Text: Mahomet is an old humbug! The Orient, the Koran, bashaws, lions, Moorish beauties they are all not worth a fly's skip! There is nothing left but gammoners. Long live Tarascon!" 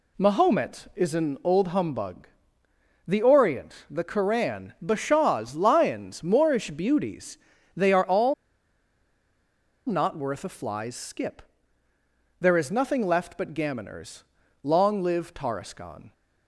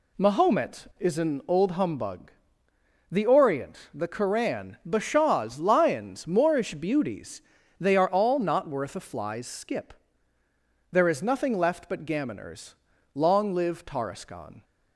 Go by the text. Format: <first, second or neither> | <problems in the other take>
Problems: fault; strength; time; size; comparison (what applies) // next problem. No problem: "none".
second | pauses between "beauties" and "they"; at 7.3 s; 0.40 s long; also in the second // pauses between "all" and "not"; strong; at 8.3 s; 1.5 s long